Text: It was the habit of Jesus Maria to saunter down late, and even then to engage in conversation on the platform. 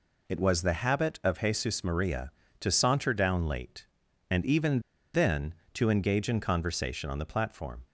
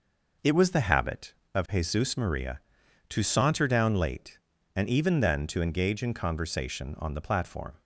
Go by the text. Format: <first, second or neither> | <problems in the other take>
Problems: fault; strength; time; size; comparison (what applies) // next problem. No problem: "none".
second | pauses between "even" and "then"; slight; at 4.7 s; 0.34 s long